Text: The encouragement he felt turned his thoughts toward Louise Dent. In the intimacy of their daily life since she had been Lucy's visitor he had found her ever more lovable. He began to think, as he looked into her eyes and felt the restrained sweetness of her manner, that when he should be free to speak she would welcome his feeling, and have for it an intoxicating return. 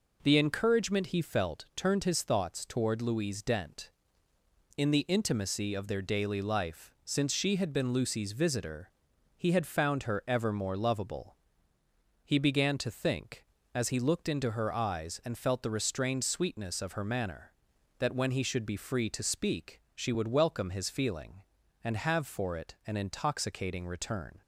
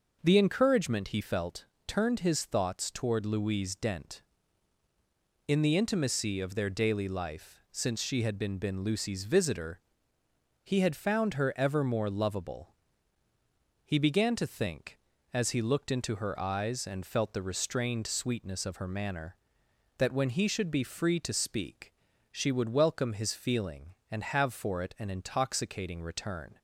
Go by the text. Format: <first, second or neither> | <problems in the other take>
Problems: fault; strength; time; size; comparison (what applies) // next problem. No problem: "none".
first | pauses between "felt" and "turned"; slight; at 1.6 s; 0.20 s long // says "been" twice; at 8.5 s // pauses between "visitor" and "he"; noticeable; at 9.7 s; 0.84 s long; also in the first // pauses between "speak" and "she"; at 21.9 s; 0.40 s long